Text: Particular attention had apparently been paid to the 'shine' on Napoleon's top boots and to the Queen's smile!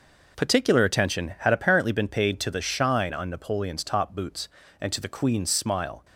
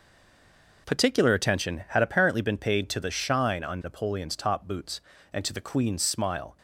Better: first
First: none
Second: stays silent before the first word; slight; until 0.8 s; 0.8 s long

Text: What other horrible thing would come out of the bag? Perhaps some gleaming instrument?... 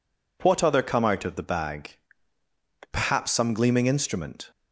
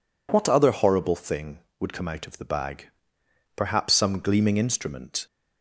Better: second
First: skips "horrible thing would"; at 0.8 s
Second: none

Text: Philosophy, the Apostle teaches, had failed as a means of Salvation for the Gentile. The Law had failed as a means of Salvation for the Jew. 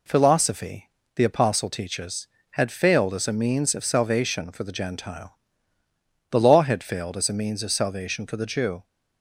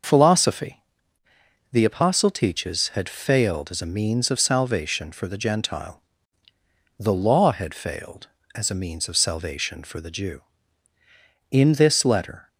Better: first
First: none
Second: goes on to say "In this Letter"; noticeable; from 11.4 s on; 0.98 s long

